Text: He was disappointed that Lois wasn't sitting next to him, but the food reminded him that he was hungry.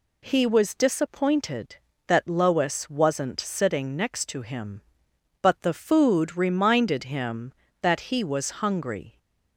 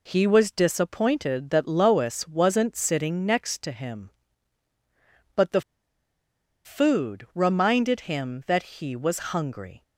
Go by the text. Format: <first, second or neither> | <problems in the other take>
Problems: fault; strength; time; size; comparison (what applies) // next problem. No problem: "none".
first | pauses between "the" and "food"; at 5.6 s; 1.0 s long